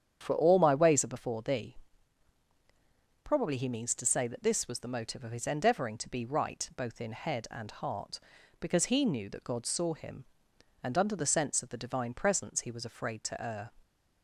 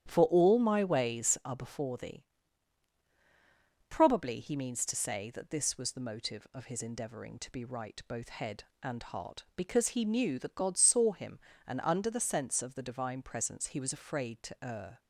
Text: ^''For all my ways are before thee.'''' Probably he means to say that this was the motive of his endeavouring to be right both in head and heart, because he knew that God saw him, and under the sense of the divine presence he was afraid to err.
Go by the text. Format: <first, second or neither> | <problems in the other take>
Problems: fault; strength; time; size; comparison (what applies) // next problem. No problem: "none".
first | starts louder than the rest; strong; until 1.1 s; 10.5 dB; strong in the first // skips "in"; at 8.2 s